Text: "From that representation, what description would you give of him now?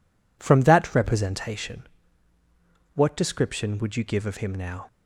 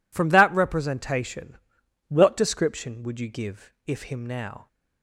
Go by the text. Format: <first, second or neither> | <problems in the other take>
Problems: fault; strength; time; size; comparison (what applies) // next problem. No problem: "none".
first | says "if" for "of"; at 3.8 s